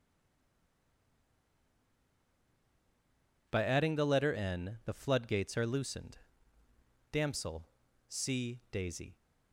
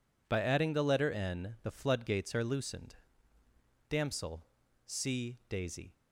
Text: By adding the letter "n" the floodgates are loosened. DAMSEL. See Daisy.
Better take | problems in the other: second | stays silent before the first word; strong; until 3.4 s; 3.4 s long

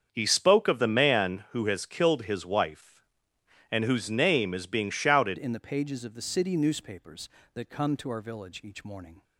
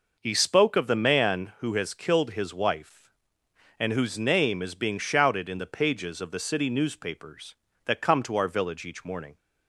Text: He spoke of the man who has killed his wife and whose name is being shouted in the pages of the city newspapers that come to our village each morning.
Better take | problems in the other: second | starts louder than the rest; strong; until 1.1 s; 7 dB // changes voice at "in"; from 5.3 s on; 3.9 s long

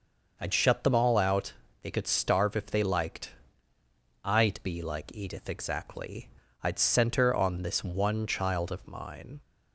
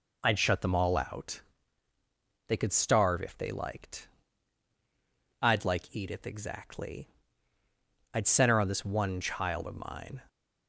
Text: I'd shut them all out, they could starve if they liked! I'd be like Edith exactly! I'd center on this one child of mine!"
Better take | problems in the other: first | skips "be"; at 5.6 s

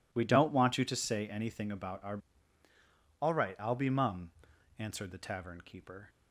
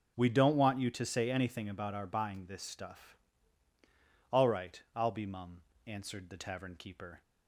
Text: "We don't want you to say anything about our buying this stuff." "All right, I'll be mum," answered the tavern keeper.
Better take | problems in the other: second | skips "buying this stuff"; at 2.6 s

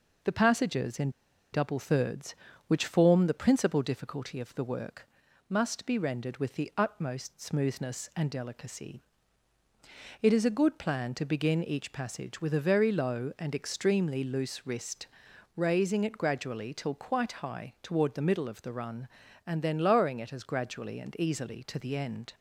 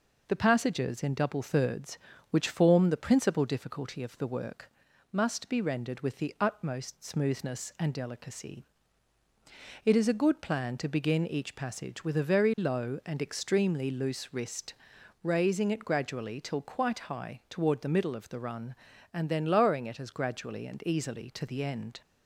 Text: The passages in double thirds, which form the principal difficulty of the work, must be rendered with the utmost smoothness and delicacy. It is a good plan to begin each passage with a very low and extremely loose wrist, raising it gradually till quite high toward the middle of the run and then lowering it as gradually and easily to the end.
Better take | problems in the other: second | pauses between "in" and "double"; at 1.0 s; 0.43 s long

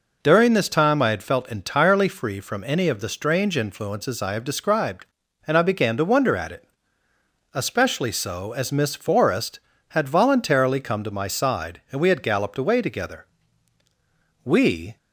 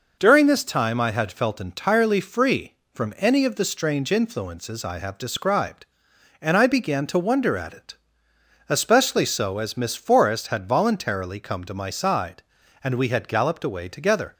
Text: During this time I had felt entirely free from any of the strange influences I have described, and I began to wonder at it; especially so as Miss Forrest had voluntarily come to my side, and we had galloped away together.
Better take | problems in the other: second | goes on to say "We"; from 14.4 s on; 0.54 s long

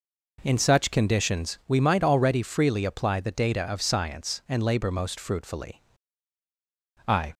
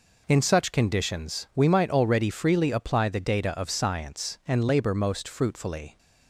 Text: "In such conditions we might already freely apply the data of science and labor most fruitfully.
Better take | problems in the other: second | goes on to say "I"; slight; from 7.0 s on; 0.28 s long

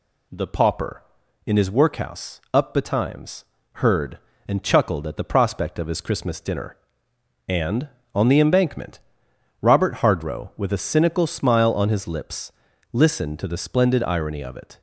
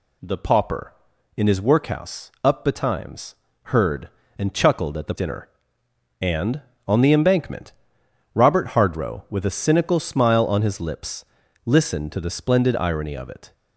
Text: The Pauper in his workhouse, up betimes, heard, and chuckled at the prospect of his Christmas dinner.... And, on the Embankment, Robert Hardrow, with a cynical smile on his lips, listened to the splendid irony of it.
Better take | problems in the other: first | skips "prospect of his Christmas"; at 5.1 s

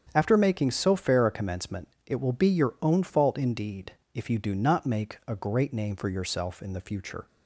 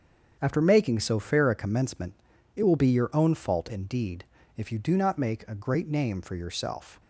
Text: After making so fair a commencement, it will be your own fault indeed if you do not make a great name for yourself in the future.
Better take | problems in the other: first | starts louder than the rest; strong; until 1.4 s; 7.5 dB; strong in the first // pauses between "indeed" and "if"; slight; at 4.2 s; 0.32 s long; slight in the first // stops before "in the future"; at 6.9 s

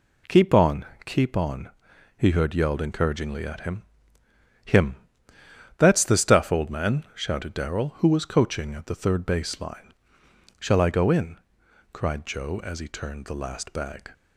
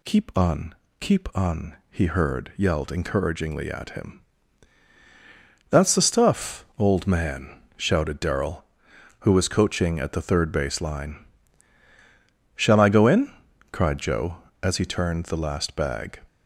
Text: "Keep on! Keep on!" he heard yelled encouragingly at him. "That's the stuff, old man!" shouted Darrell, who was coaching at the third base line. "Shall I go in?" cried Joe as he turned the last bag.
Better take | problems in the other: second | says "him" twice; at 4.6 s

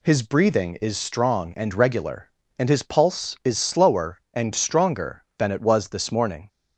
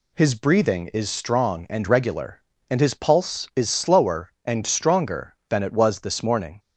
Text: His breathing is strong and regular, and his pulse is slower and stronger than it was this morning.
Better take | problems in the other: neither | none

